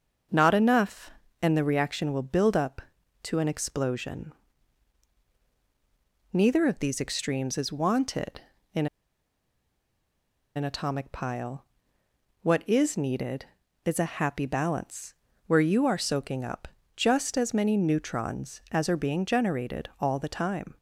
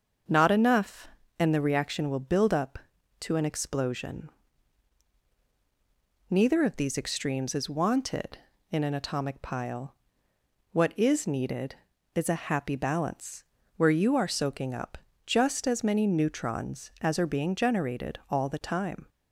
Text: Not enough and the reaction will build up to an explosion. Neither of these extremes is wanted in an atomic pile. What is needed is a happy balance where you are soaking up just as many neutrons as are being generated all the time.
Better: second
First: starts louder than the rest; until 1.6 s; 6.5 dB // pauses between "in" and "an"; strong; at 8.8 s; 1.7 s long // pauses between "balance" and "where"; slight; at 15.1 s; 0.32 s long // pauses between "up" and "just"; slight; at 16.6 s; 0.28 s long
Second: starts louder than the rest; until 1.6 s; 6.5 dB // pauses between "balance" and "where"; slight; at 13.4 s; 0.32 s long // pauses between "up" and "just"; slight; at 14.9 s; 0.28 s long

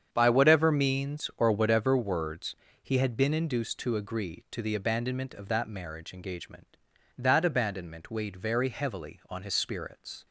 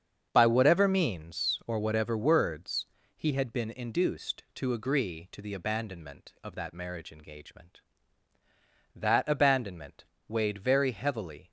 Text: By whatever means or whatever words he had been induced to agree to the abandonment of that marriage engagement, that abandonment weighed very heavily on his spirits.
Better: first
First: starts louder than the rest; strong; until 1.1 s; 8 dB // pauses between "words" and "he"; slight; at 2.5 s; 0.27 s long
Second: starts louder than the rest; strong; until 1.3 s; 7.5 dB // pauses between "words" and "he"; slight; at 2.8 s; 0.30 s long // pauses between "abandonment" and "weighed"; slight; at 10.0 s; 0.24 s long // stops before "on his spirits"; at 11.4 s

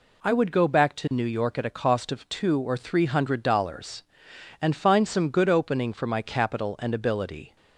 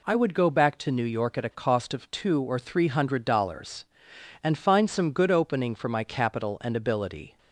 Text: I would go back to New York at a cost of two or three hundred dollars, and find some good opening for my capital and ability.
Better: neither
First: none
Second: none

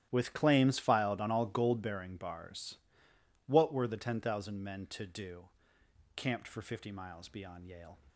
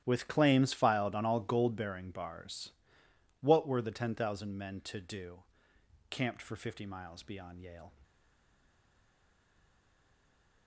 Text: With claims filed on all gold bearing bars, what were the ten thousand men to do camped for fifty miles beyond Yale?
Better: first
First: starts louder than the rest; strong; until 1.1 s; 12 dB // pauses between "do" and "camped"; noticeable; at 5.4 s; 0.68 s long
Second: starts louder than the rest; strong; until 1.0 s; 12 dB // pauses between "do" and "camped"; noticeable; at 5.4 s; 0.68 s long // stays silent after the last word; strong; from 8.0 s on; 2.6 s long

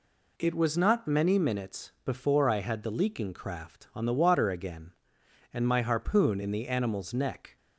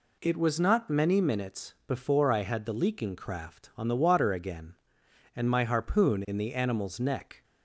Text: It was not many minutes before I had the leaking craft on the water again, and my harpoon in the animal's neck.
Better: neither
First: none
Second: none

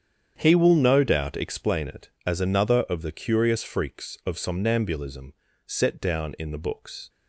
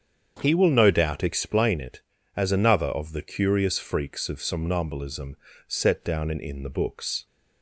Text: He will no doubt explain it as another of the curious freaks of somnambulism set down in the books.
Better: first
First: starts louder than the rest; strong; until 1.3 s; 8.5 dB // pauses between "somnambulism" and "set"; slight; at 5.3 s; 0.32 s long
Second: starts louder than the rest; strong; until 1.4 s; 7.5 dB // pauses between "somnambulism" and "set"; slight; at 5.3 s; 0.30 s long // says "in" twice; at 6.3 s

